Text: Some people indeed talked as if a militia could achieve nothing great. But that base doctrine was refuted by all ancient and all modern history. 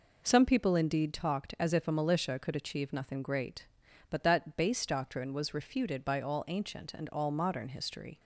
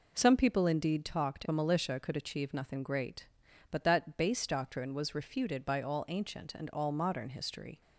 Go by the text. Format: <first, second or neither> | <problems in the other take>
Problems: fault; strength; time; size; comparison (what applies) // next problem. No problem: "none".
first | skips "as if"; at 1.4 s